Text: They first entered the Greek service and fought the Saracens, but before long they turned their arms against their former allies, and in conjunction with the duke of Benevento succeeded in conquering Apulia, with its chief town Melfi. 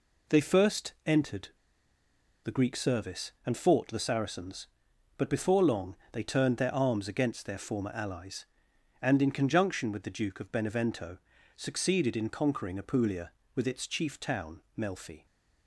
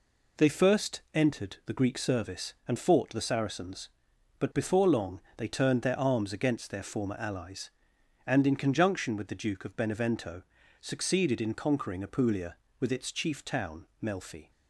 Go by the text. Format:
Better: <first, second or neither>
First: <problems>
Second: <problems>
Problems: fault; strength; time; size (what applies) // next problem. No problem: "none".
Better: second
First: pauses between "entered" and "the"; noticeable; at 1.4 s; 0.94 s long // pauses between "long" and "they"; slight; at 5.9 s; 0.16 s long // pauses between "Benevento" and "succeeded"; slight; at 11.1 s; 0.36 s long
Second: pauses between "long" and "they"; slight; at 5.1 s; 0.16 s long // pauses between "Benevento" and "succeeded"; slight; at 10.4 s; 0.36 s long